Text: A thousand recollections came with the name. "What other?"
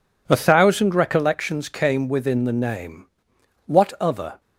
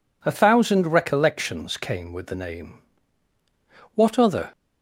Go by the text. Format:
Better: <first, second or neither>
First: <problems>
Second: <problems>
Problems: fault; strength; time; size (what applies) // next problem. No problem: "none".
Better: second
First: says "within" for "with"; at 2.0 s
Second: none